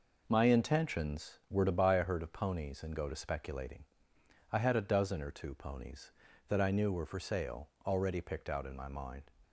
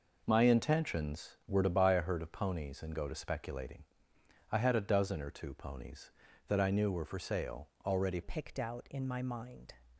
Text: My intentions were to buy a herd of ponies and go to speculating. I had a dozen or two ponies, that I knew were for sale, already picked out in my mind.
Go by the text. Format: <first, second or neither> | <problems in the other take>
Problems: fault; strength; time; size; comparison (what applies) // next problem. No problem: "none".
first | changes voice at "picked"; from 8.2 s on; 1.5 s long